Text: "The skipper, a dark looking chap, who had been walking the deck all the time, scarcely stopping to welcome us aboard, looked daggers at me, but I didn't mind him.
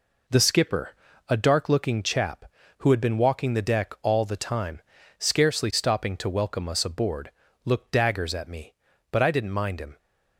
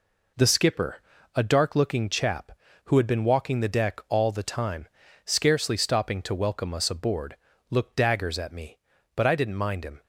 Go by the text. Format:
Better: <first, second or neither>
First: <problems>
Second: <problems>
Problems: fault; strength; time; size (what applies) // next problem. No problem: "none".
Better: neither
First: none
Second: none